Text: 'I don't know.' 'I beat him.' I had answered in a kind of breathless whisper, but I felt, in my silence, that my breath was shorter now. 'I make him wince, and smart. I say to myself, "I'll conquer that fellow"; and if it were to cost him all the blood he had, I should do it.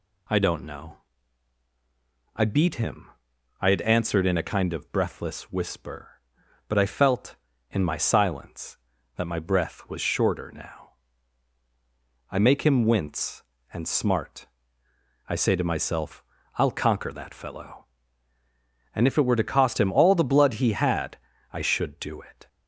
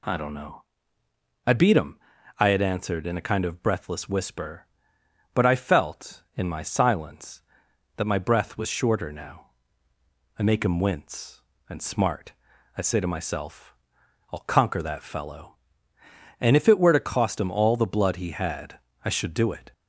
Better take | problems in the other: neither | none

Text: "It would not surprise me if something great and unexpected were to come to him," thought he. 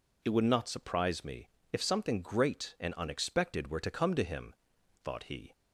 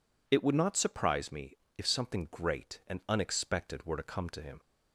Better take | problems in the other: first | pauses between "me" and "if"; slight; at 1.5 s; 0.22 s long; slight in the first // stops before "thought he"; at 4.5 s

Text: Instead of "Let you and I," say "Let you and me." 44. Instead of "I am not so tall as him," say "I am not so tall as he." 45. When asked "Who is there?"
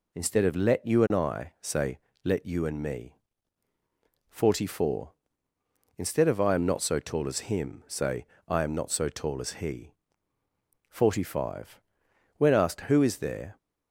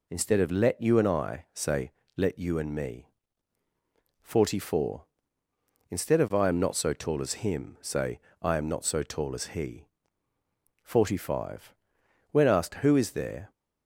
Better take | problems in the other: neither | pauses between "say" and "Let"; slight; the same in both // pauses between "say" and "I"; slight; the same in both

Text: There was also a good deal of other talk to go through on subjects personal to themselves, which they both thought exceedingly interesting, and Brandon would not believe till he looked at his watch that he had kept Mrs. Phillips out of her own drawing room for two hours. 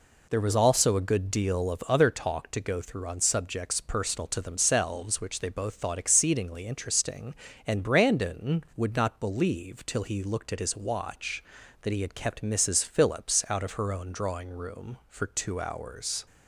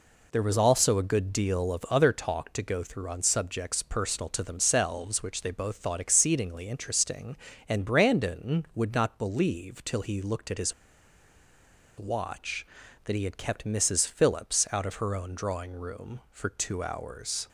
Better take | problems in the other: first | pauses between "his" and "watch"; strong; at 10.7 s; 1.2 s long

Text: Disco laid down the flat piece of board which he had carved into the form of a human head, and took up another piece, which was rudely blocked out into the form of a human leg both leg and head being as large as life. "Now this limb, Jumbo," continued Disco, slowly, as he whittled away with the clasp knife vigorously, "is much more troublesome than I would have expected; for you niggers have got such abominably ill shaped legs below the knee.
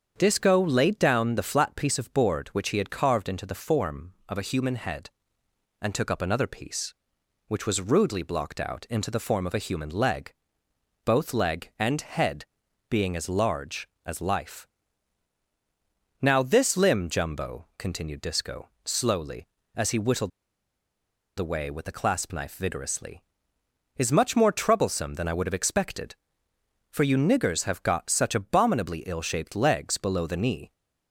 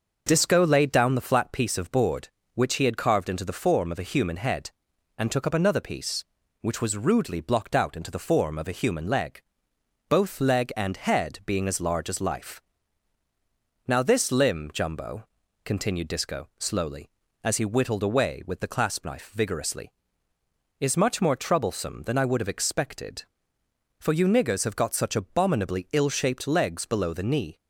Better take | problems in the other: second | starts louder than the rest; strong; until 1.1 s; 7.5 dB; noticeable in the second // pauses between "leg" and "both"; noticeable; at 10.3 s; 0.72 s long; noticeable in the second // pauses between "head" and "being"; noticeable; at 12.4 s; 0.46 s long // pauses between "whittled" and "away"; at 20.3 s; 1.0 s long

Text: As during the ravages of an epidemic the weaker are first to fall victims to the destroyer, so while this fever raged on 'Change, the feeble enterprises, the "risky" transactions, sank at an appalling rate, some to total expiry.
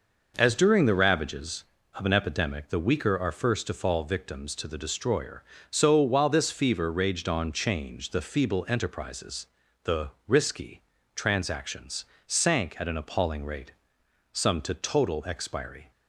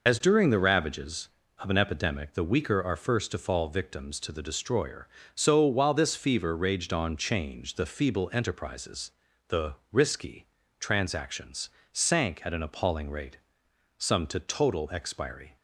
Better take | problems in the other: first | loses the start of "As"; at 0.0 s; 80 ms // pauses between "the" and "risky"; slight; at 9.7 s; 0.18 s long; slight in the first // pauses between "risky" and "transactions"; slight; at 10.4 s; 0.34 s long; slight in the first

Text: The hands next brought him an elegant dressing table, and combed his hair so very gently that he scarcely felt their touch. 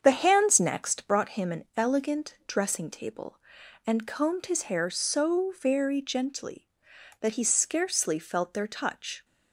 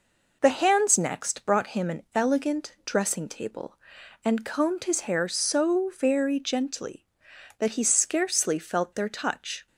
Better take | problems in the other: second | starts louder than the rest; strong; until 1.2 s; 7.5 dB

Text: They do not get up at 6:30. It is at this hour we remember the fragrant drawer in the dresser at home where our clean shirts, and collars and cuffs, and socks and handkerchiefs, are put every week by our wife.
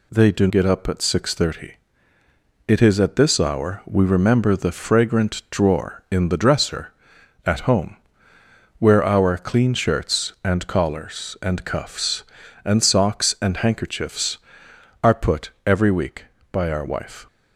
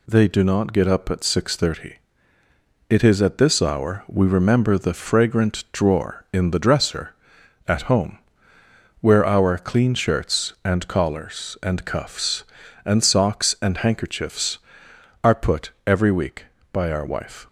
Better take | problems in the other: second | skips "not"; at 0.4 s // pauses between "home" and "where"; noticeable; at 7.9 s; 0.82 s long; noticeable in the second

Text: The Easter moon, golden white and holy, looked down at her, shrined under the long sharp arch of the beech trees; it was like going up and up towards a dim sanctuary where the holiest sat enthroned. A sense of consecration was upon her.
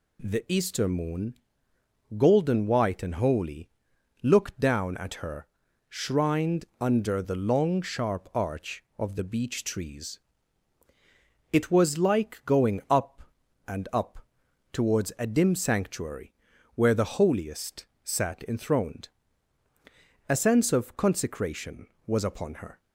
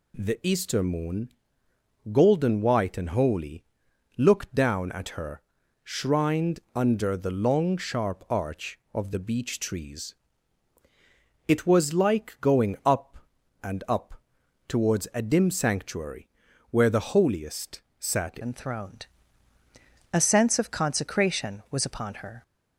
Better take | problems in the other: first | pauses between "up" and "towards"; noticeable; at 14.2 s; 0.48 s long; noticeable in the first // pauses between "sanctuary" and "where"; at 16.2 s; 0.40 s long; also in the first // pauses between "holiest" and "sat"; slight; at 17.8 s; 0.18 s long; slight in the first // changes voice at "enthroned"; from 18.4 s on; 4.0 s long

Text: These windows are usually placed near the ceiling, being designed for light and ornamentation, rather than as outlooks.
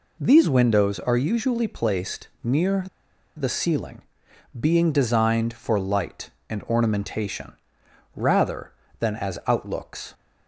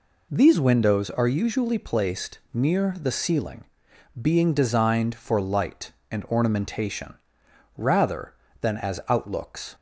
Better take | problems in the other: second | pauses between "placed" and "near"; slight; at 2.2 s; 0.16 s long; slight in the second // pauses between "near" and "the"; noticeable; at 2.8 s; 0.52 s long

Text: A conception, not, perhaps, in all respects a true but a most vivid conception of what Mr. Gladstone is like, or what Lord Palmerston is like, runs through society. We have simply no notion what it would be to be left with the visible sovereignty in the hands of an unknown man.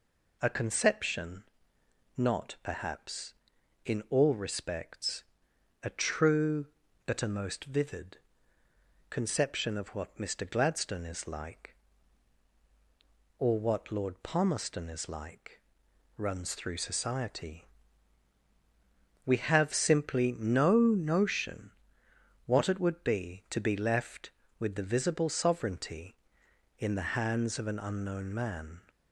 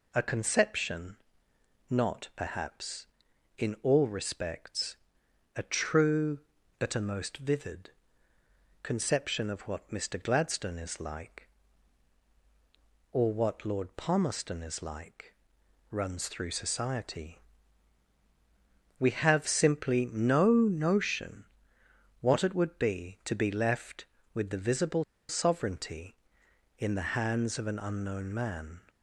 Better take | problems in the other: first | pauses between "respects" and "a"; noticeable; at 4.9 s; 0.58 s long; noticeable in the first // pauses between "vivid" and "conception"; noticeable; at 7.8 s; 0.92 s long; noticeable in the first // pauses between "notion" and "what"; noticeable; at 21.4 s; 0.78 s long; noticeable in the first // pauses between "visible" and "sovereignty"; slight; at 25.0 s; 0.25 s long

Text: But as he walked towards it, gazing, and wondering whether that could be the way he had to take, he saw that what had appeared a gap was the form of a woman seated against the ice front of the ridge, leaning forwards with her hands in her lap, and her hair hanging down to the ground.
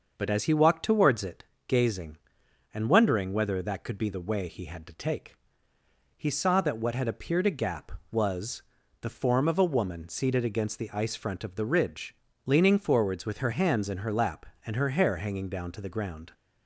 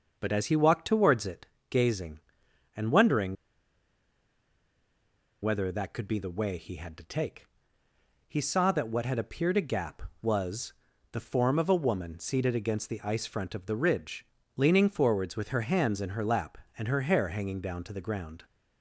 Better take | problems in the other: first | starts louder than the rest; until 1.2 s; 6.5 dB; also in the first // pauses between "wondering" and "whether"; strong; at 3.3 s; 2.0 s long // pauses between "was" and "the"; at 10.7 s; 0.38 s long; also in the first

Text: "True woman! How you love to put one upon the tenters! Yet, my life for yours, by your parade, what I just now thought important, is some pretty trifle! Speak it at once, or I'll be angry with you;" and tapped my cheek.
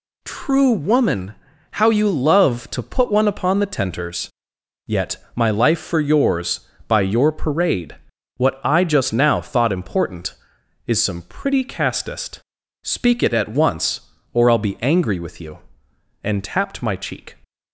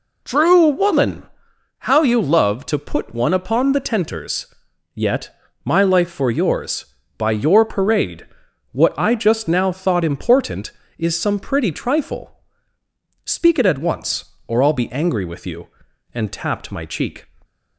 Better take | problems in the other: second | says "castest" for "trifle"; at 11.6 s

